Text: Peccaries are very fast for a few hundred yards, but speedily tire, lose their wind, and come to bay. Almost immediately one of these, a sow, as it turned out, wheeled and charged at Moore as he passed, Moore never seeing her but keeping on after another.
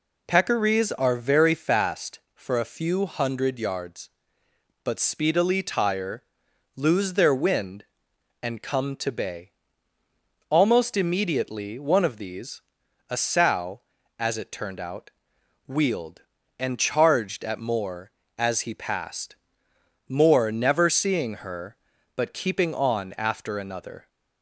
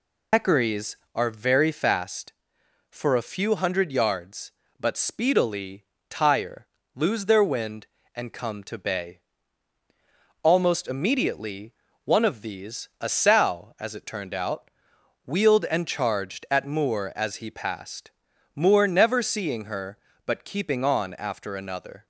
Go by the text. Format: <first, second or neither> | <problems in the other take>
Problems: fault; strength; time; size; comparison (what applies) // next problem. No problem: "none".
first | loses the start of "Peccaries"; at 0.3 s; 110 ms // pauses between "speedily" and "tire"; slight; at 5.8 s; 0.26 s long // pauses between "immediately" and "one"; slight; at 11.7 s; 0.32 s long